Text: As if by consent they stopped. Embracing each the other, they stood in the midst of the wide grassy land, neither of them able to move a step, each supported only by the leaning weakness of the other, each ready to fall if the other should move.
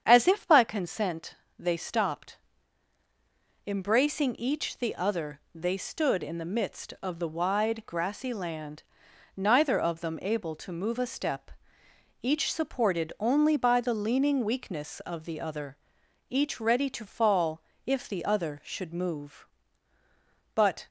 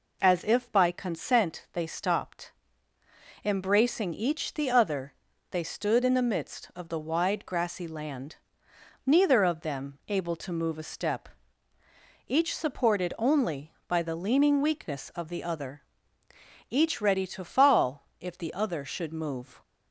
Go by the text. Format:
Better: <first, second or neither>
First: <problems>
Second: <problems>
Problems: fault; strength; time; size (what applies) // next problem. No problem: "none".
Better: second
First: starts louder than the rest; strong; until 1.0 s; 8 dB // pauses between "consent" and "they"; slight; at 1.3 s; 0.22 s long // pauses between "fall" and "if"; slight; at 17.6 s; 0.24 s long // goes on to say "But"; slight; from 20.5 s on; 0.32 s long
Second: none